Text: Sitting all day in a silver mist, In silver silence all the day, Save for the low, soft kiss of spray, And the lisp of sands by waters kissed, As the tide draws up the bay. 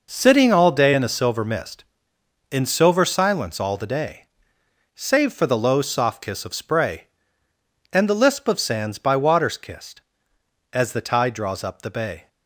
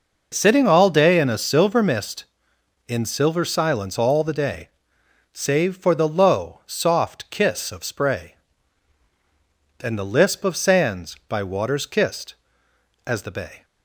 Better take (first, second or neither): first